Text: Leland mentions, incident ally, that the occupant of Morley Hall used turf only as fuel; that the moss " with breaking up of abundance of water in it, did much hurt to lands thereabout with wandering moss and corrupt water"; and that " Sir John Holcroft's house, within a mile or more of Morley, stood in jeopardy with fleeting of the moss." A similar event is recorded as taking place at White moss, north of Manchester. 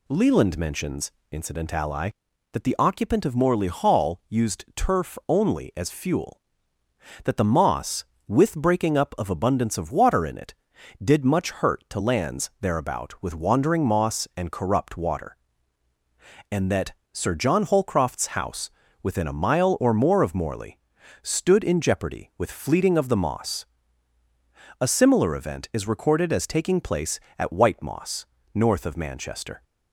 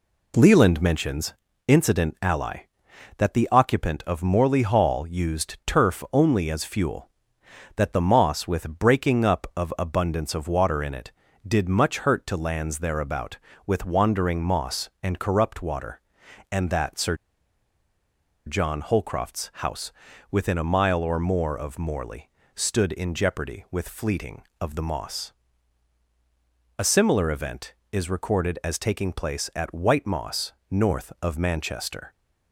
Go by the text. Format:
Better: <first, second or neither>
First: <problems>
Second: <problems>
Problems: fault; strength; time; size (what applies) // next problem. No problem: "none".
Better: first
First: none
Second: pauses between "Sir" and "John"; strong; at 17.1 s; 1.3 s long